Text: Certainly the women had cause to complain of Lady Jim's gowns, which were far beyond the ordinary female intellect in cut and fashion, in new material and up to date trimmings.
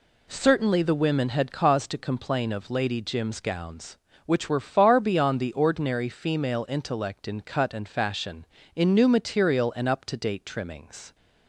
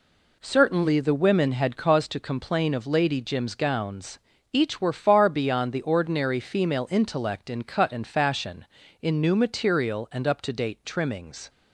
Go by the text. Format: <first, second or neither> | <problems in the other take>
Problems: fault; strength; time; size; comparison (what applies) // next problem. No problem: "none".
first | says "each" for "which"; at 4.5 s